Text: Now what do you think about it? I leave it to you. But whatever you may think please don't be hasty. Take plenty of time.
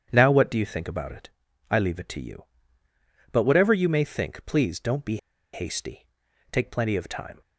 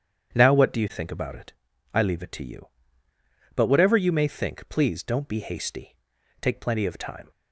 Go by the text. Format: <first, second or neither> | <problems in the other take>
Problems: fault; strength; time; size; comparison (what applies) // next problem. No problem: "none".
second | starts louder than the rest; strong; until 1.1 s; 8.5 dB; strong in the second // pauses between "be" and "hasty"; at 5.1 s; 0.36 s long